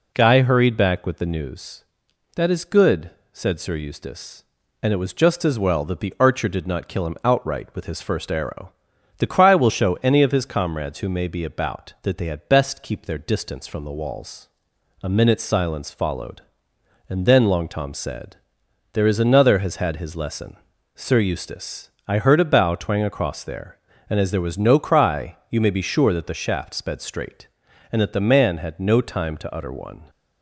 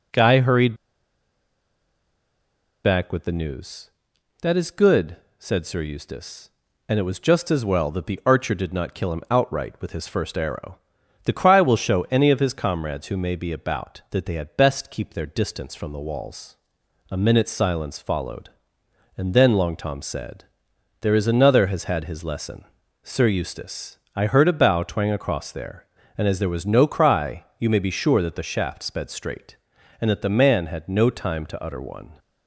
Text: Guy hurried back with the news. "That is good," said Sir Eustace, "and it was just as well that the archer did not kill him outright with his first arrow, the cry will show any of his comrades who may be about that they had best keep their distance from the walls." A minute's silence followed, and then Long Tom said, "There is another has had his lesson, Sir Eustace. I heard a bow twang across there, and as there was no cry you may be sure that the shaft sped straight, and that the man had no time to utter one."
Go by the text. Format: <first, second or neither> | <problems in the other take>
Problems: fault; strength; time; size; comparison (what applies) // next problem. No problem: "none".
first | pauses between "hurried" and "back"; strong; at 0.7 s; 2.0 s long // pauses between "cry" and "you"; slight; at 27.4 s; 0.16 s long; slight in the first